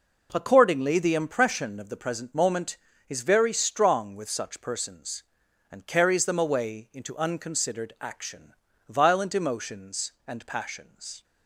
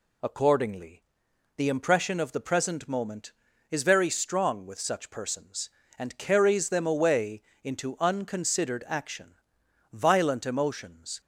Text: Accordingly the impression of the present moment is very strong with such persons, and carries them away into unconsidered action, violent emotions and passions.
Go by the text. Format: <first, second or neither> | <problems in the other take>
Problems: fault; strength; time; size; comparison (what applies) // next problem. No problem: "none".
first | pauses between "Accordingly" and "the"; noticeable; at 1.0 s; 0.54 s long // pauses between "away" and "into"; slight; at 7.4 s; 0.22 s long // stops before "and passions"; at 11.2 s